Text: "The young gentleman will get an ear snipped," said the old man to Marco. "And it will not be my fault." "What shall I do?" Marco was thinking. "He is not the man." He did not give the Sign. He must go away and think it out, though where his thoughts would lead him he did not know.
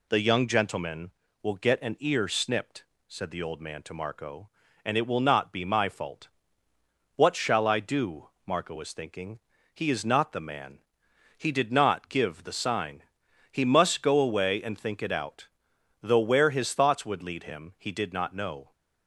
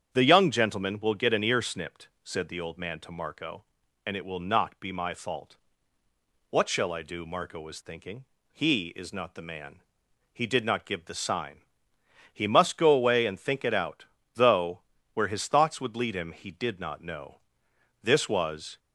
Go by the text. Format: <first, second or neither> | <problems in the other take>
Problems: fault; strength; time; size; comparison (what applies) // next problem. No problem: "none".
first | starts louder than the rest; strong; until 1.1 s; 8 dB // pauses between "though" and "where"; slight; at 14.8 s; 0.32 s long // goes on to say "This was"; noticeable; from 18.0 s on; 0.78 s long